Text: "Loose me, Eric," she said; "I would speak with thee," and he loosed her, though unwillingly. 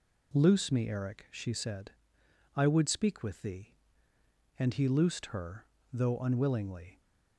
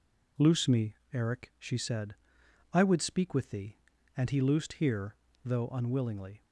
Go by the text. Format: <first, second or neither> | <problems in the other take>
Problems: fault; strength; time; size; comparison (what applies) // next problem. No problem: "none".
first | says "here" for "her"; at 4.7 s